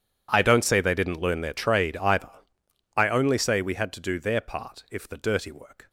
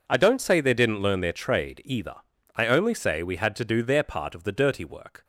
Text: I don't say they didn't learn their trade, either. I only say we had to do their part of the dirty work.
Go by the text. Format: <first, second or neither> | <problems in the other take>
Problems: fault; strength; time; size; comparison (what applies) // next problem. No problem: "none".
second | says "if" for "of"; at 4.9 s